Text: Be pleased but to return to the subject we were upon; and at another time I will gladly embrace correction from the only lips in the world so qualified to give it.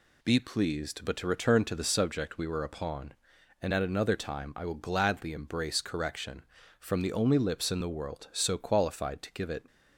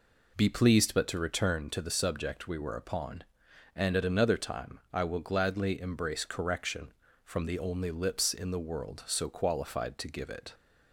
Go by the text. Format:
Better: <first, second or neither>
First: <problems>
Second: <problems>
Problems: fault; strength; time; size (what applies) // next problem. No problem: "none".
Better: neither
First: none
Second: none